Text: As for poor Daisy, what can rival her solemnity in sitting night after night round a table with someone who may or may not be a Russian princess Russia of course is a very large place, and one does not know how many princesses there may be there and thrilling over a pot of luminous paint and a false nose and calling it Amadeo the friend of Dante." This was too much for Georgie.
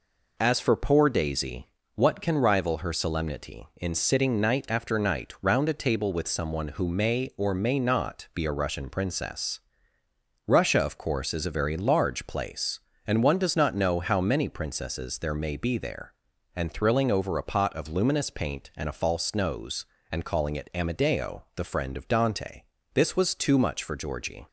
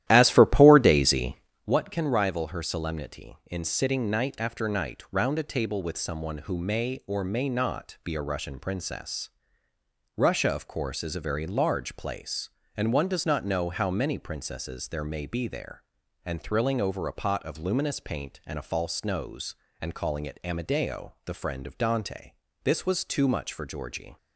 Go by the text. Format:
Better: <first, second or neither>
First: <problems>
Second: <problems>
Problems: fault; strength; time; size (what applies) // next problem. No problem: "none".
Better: first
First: pauses between "princess" and "Russia"; noticeable; at 9.6 s; 0.84 s long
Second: starts louder than the rest; strong; until 1.7 s; 13 dB // pauses between "princess" and "Russia"; noticeable; at 9.3 s; 0.84 s long